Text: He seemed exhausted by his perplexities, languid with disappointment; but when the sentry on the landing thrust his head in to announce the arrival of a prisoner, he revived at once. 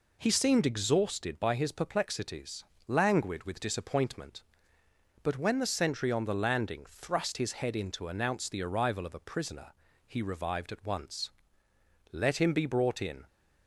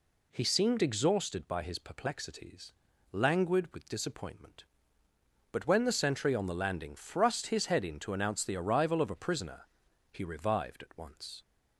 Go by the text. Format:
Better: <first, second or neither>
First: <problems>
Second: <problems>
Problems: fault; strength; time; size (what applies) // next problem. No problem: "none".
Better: second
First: goes on to say "Let him be brought in"; noticeable; from 12.1 s on; 1.1 s long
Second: none